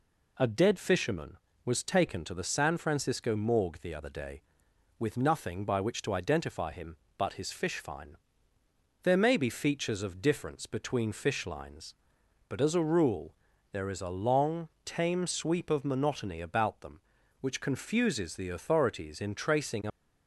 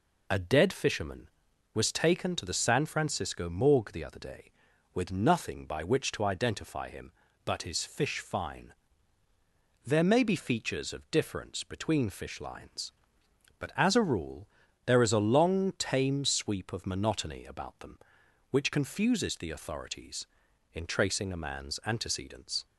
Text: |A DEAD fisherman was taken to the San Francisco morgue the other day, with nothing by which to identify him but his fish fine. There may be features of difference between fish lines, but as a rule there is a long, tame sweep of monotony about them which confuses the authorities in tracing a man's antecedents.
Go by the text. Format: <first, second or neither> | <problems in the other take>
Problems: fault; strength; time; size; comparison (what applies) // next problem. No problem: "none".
second | pauses between "rule" and "there"; at 13.3 s; 0.38 s long; slight in the second // stops before "man's antecedents"; at 19.9 s